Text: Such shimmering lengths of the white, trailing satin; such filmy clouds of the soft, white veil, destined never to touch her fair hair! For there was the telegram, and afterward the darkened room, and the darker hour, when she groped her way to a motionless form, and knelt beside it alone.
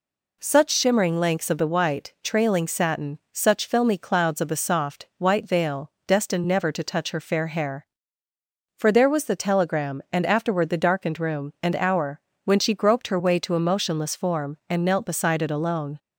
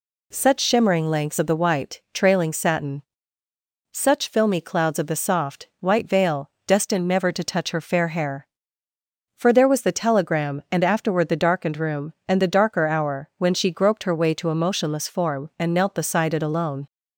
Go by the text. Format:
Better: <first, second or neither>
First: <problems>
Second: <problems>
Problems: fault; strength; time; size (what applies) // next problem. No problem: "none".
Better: second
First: skips "the darker"; at 11.7 s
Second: none